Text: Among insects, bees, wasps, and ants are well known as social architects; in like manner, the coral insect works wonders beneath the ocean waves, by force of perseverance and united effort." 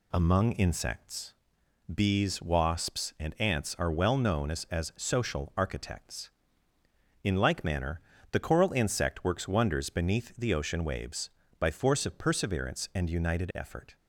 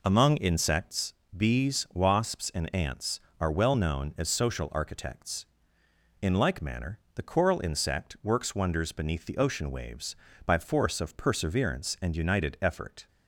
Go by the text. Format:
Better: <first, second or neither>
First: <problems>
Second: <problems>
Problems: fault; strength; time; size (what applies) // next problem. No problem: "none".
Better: second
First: says "as" twice; at 4.6 s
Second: none